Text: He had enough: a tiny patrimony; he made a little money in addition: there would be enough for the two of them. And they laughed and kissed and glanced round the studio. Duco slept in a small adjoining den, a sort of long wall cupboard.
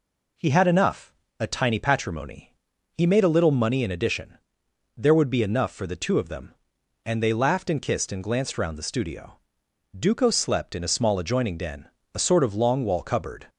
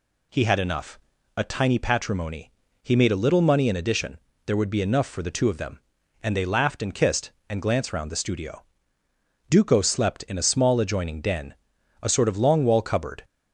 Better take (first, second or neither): neither